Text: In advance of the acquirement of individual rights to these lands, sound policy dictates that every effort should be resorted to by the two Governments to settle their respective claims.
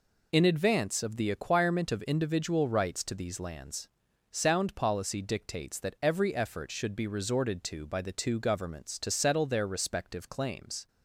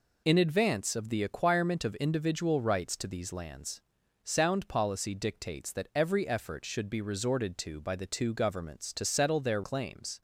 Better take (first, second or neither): first